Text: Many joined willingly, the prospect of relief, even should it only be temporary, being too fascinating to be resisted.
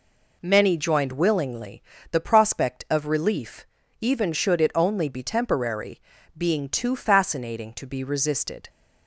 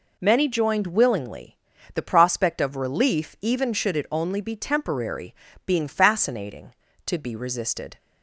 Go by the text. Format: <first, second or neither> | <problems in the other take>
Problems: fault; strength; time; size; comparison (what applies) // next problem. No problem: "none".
first | skips "too"; at 5.8 s